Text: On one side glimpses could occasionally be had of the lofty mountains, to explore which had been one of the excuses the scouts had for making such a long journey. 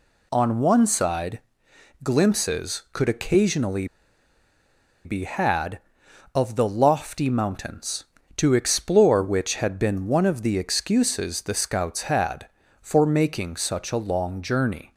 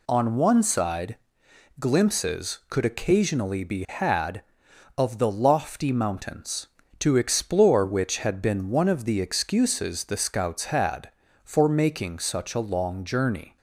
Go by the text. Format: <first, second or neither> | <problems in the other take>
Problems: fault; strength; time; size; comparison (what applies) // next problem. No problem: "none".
second | pauses between "side" and "glimpses"; noticeable; at 1.4 s; 0.62 s long; noticeable in the second // pauses between "occasionally" and "be"; at 3.8 s; 1.1 s long